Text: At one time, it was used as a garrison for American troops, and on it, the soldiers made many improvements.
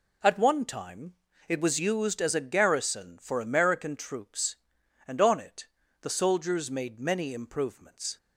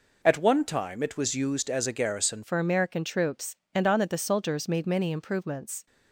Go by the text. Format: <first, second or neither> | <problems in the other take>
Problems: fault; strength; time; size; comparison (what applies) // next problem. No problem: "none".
first | changes voice at "for"; from 2.4 s on; 3.4 s long